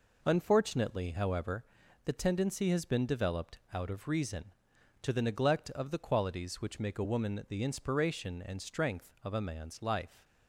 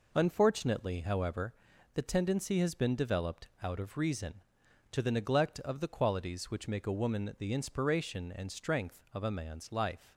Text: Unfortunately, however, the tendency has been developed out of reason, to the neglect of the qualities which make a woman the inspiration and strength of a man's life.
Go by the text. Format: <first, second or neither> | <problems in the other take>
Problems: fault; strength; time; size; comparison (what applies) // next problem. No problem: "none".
neither | pauses between "developed" and "out"; slight; the same in both